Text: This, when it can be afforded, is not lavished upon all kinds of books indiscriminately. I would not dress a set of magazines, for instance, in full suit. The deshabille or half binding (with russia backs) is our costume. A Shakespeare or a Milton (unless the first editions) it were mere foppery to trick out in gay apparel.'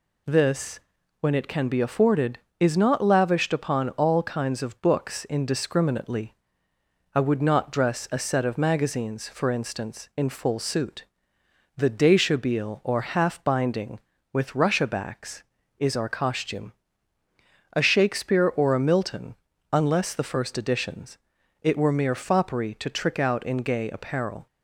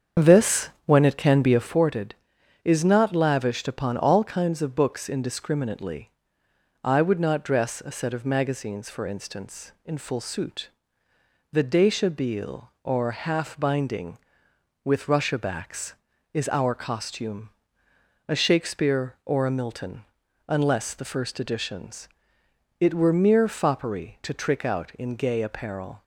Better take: first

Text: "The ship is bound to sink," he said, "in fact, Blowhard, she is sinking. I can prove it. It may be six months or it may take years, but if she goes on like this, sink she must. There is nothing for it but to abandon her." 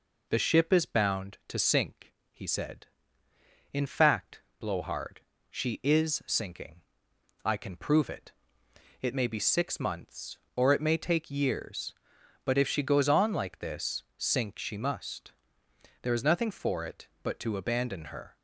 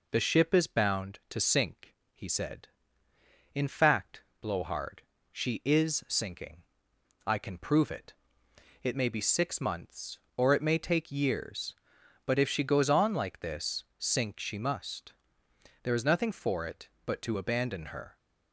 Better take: neither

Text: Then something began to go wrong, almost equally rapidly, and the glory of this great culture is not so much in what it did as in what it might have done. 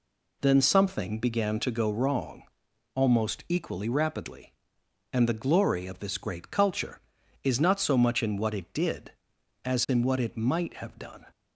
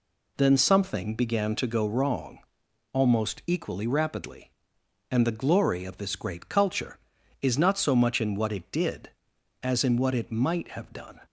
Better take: neither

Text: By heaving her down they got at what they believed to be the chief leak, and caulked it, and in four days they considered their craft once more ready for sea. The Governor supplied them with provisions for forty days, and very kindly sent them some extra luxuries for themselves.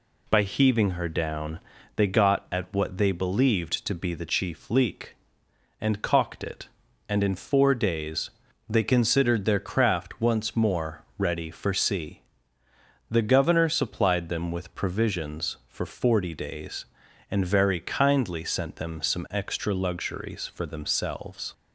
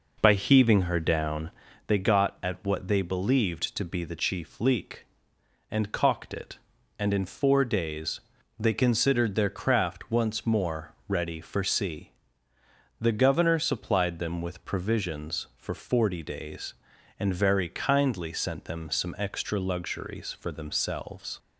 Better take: first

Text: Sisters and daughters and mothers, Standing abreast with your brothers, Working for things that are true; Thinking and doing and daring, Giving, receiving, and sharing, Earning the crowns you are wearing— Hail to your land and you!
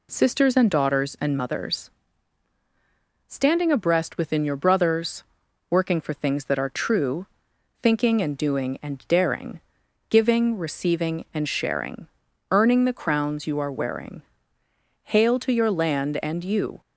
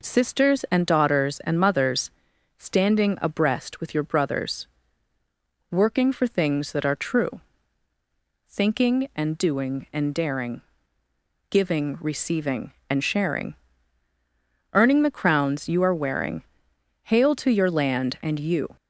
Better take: second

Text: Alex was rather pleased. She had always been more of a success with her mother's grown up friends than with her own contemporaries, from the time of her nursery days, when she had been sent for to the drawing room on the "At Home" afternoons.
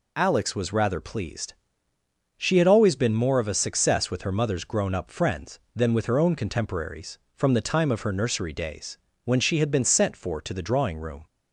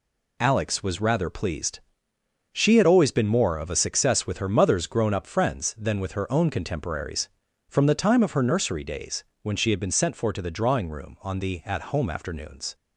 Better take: second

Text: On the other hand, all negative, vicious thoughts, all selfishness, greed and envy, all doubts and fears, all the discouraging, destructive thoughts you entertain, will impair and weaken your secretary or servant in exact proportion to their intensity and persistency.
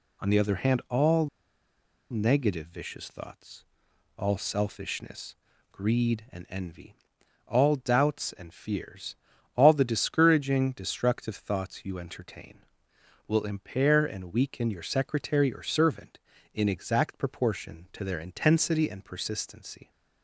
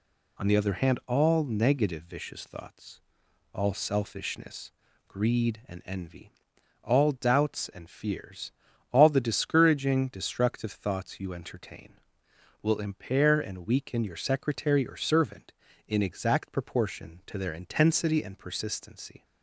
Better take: second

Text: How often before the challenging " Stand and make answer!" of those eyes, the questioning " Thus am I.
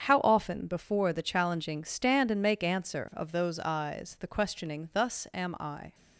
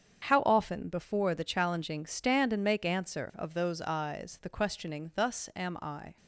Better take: neither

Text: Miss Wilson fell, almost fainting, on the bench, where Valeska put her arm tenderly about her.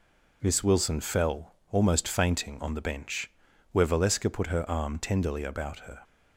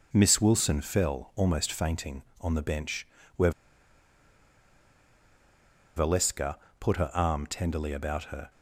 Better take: first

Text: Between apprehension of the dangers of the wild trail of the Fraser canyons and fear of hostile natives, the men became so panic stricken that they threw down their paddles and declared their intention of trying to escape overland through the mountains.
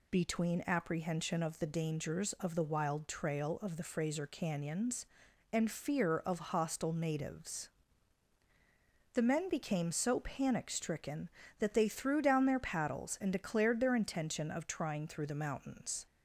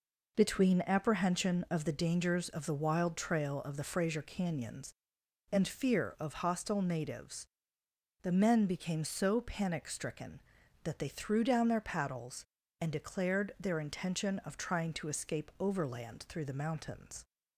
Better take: second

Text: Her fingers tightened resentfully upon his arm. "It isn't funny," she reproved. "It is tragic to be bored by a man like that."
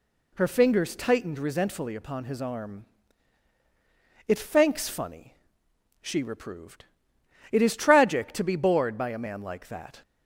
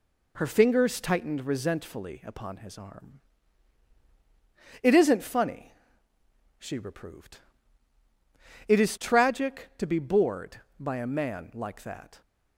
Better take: second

